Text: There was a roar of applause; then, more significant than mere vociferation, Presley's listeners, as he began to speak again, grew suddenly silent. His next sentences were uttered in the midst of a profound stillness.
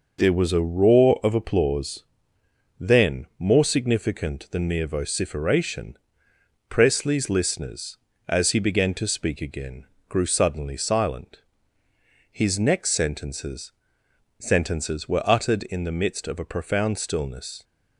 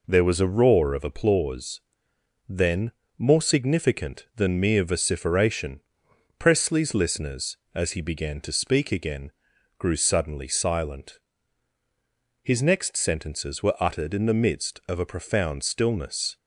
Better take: second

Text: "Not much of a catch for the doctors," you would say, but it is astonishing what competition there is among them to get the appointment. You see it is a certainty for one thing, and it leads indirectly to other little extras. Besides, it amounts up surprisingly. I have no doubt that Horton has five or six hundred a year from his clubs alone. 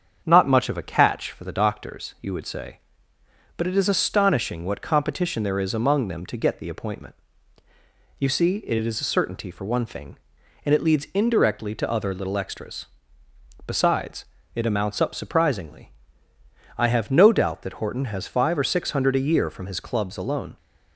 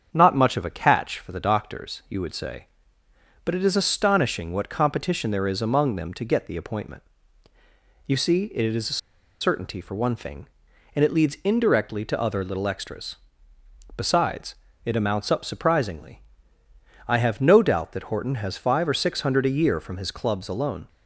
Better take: first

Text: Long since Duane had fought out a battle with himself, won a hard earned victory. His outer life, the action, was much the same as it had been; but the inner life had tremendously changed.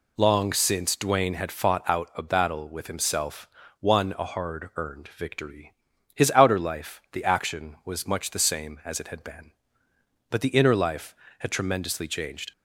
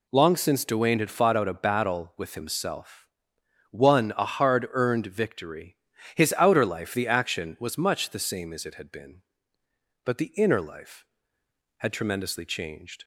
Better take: neither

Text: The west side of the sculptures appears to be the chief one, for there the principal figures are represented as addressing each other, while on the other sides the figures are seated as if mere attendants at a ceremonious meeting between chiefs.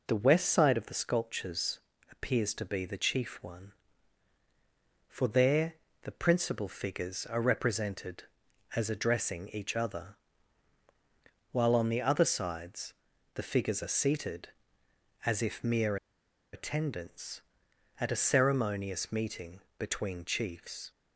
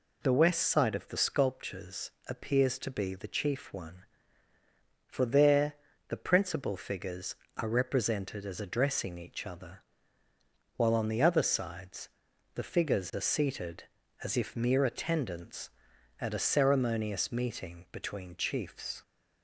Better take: second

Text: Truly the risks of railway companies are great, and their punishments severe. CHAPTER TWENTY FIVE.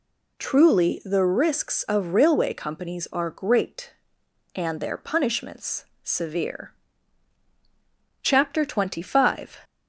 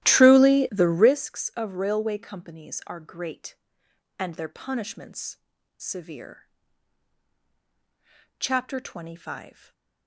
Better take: first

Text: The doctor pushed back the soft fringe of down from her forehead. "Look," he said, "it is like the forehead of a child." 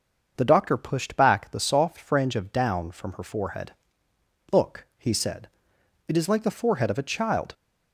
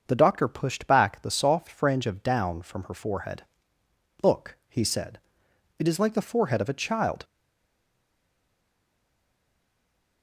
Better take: first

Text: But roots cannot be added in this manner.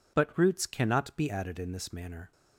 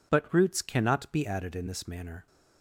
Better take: neither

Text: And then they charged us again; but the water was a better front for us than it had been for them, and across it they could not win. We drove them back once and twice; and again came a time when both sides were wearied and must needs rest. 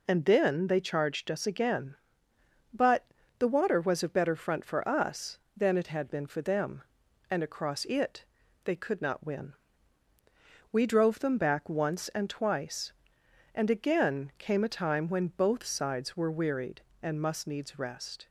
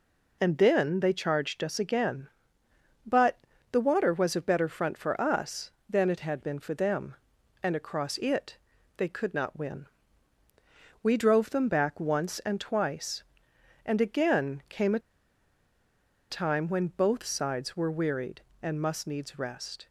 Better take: first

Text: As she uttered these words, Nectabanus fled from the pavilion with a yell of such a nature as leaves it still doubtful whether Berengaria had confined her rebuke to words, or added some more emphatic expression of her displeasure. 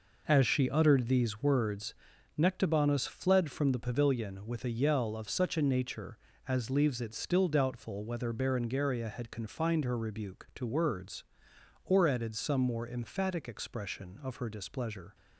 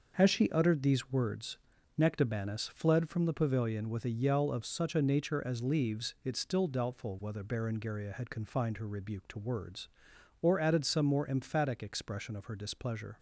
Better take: neither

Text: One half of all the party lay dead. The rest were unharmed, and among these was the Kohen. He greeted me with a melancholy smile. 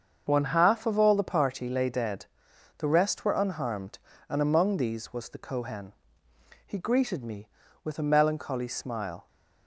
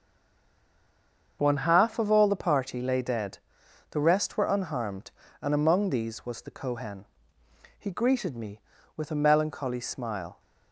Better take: first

